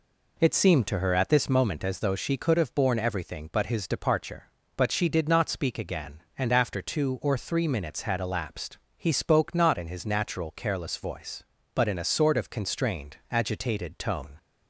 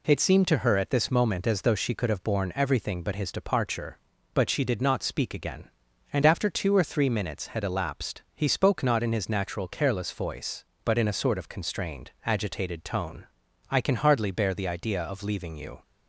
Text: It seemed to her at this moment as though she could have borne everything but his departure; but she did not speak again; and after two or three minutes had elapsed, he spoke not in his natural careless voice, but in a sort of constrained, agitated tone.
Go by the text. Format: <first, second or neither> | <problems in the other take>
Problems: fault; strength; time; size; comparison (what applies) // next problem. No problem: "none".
first | goes on to say "I can hardly bear the idea of leaving you"; strong; from 13.6 s on; 2.1 s long